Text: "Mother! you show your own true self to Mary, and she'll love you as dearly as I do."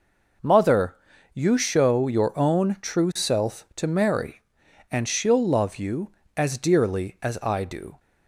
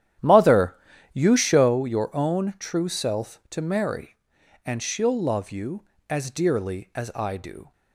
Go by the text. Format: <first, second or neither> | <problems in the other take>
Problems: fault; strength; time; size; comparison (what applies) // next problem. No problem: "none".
first | starts louder than the rest; strong; until 1.8 s; 11 dB